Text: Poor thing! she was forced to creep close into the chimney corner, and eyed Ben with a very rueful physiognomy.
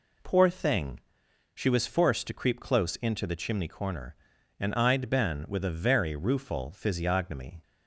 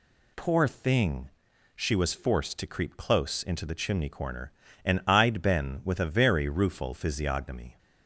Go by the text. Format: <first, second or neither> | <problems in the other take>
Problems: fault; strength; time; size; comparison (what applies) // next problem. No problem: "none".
neither | none